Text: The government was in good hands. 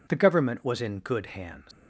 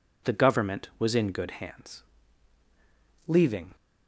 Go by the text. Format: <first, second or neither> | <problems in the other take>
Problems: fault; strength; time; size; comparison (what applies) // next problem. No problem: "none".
first | goes on to say "Leaving"; slight; from 3.2 s on; 0.48 s long